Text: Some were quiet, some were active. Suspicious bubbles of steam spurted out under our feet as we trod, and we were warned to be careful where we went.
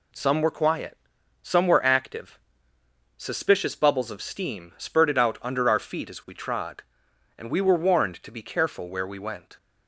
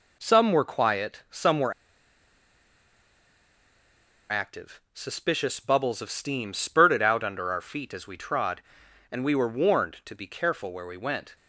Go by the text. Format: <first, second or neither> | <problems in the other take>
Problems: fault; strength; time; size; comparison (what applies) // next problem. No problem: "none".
first | pauses between "were" and "active"; strong; at 1.7 s; 2.5 s long